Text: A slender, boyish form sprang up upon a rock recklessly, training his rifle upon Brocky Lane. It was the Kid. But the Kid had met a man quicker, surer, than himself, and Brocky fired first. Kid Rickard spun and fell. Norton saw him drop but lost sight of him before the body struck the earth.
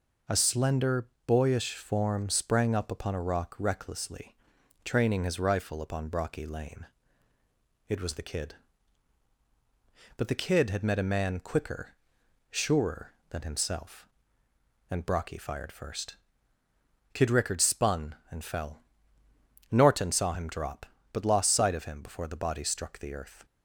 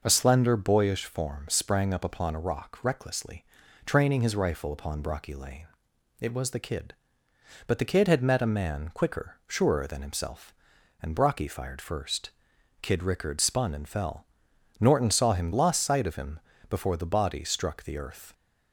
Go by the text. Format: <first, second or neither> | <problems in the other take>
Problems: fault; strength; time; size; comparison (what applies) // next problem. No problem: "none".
first | skips "drop but"; at 15.5 s // pauses between "him" and "before"; slight; at 16.3 s; 0.32 s long